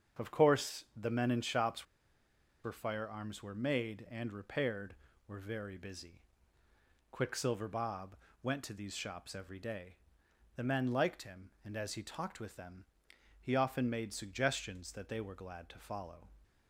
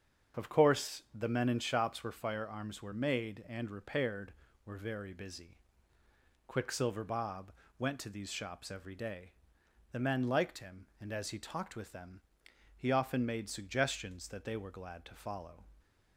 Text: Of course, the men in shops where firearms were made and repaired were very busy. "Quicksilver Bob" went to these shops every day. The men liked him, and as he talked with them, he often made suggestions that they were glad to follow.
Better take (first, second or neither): second